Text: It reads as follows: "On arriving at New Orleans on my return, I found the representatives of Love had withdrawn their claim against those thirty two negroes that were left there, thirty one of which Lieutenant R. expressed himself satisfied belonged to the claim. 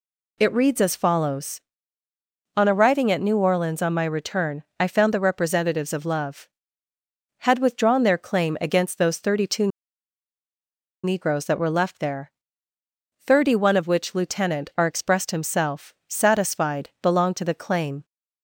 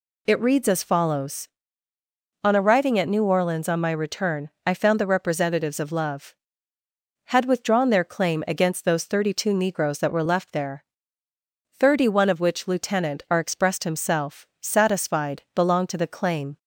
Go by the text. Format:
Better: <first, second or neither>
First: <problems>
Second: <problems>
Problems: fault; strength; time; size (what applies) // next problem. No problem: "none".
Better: second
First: pauses between "two" and "negroes"; strong; at 9.6 s; 1.3 s long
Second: none